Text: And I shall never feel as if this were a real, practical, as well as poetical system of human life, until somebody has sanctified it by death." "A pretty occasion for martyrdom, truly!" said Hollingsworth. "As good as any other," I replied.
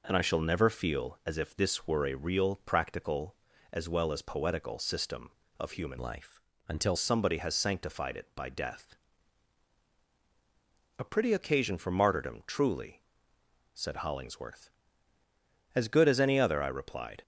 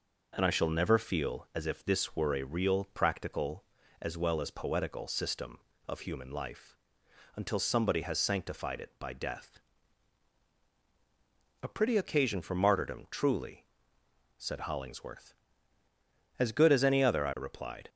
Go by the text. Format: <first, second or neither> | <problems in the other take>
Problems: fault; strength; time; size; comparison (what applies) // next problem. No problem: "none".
second | changes voice from "life" to "until"; from 5.9 to 6.9 s; 1.0 s long